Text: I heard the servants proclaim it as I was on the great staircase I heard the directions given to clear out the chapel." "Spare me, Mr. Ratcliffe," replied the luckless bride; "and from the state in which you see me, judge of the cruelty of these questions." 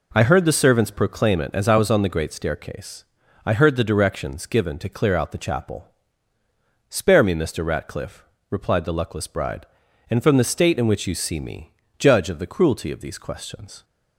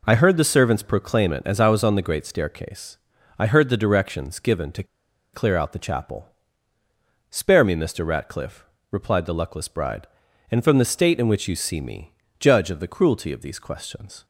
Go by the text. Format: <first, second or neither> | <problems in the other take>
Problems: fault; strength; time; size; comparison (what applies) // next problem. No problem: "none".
first | pauses between "staircase" and "I"; at 2.9 s; 0.40 s long; also in the first // pauses between "to" and "clear"; noticeable; at 4.8 s; 0.49 s long